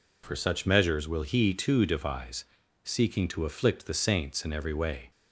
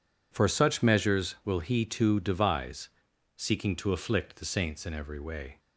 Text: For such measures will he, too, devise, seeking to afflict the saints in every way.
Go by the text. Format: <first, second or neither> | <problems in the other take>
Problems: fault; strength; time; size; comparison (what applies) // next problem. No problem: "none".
neither | none